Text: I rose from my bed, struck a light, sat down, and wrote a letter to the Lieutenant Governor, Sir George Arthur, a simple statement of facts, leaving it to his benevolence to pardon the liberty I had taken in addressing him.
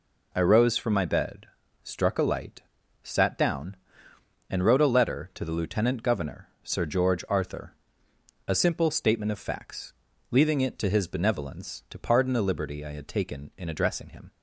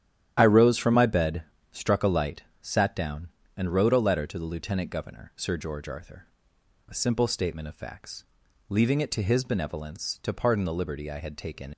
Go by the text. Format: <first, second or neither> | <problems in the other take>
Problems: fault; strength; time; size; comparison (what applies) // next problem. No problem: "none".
first | starts louder than the rest; strong; until 1.3 s; 11 dB // stops before "in addressing him"; at 11.7 s